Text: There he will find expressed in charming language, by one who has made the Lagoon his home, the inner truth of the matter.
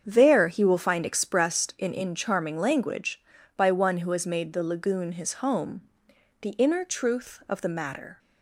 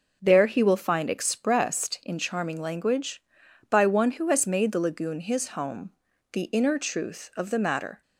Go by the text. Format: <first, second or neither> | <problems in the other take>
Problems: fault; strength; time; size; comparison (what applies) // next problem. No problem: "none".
second | starts louder than the rest; strong; until 1.0 s; 7.5 dB // says "in" twice; at 1.9 s